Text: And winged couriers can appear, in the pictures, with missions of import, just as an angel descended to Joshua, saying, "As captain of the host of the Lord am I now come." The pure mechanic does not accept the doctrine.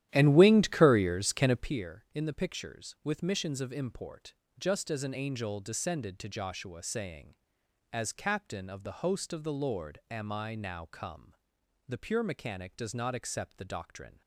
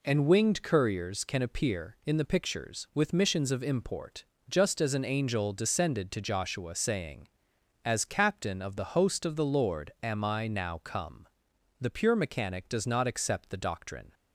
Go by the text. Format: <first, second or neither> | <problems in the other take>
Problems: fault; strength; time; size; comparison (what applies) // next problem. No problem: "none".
second | starts louder than the rest; strong; until 1.7 s; 12 dB